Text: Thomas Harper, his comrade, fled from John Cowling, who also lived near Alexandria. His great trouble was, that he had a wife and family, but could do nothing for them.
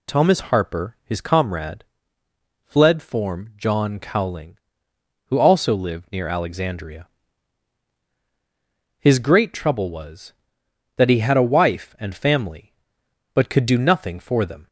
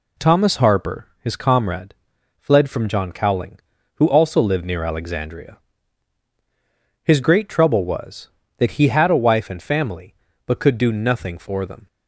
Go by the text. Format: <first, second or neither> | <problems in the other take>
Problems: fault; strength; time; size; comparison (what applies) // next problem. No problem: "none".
second | says "form" for "from"; at 3.0 s